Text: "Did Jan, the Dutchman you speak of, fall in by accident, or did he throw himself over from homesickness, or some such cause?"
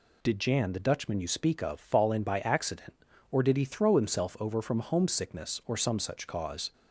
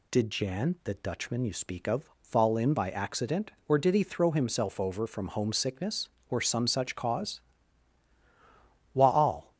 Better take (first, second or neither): first